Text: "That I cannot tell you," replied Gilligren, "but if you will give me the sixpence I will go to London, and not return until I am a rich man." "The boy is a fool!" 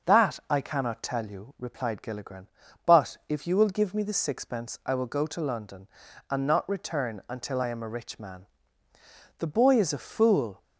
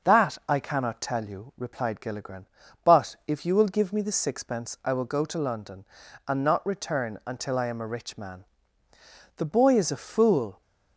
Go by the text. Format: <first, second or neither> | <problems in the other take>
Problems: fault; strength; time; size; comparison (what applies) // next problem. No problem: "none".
neither | starts louder than the rest; the same in both